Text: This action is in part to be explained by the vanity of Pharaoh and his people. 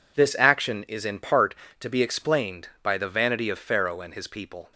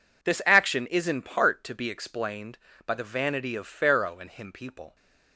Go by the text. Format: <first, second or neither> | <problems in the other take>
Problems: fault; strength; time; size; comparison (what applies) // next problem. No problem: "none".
first | says "him" for "his"; at 4.2 s